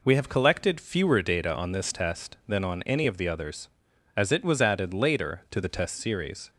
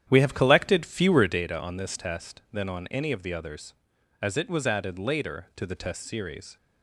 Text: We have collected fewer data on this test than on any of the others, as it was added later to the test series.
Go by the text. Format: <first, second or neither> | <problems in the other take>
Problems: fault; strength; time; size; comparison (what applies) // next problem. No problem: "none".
first | starts louder than the rest; strong; until 1.4 s; 10 dB